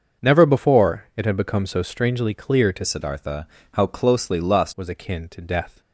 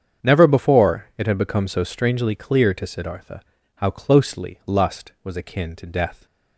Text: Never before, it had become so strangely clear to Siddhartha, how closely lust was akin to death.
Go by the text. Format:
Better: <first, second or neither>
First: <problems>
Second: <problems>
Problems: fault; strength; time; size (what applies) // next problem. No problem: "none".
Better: second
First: starts louder than the rest; until 1.3 s; 6.5 dB // changes voice from "Siddhartha" to "lust"; from 2.8 to 4.7 s; 1.9 s long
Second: starts louder than the rest; strong; until 1.3 s; 7.5 dB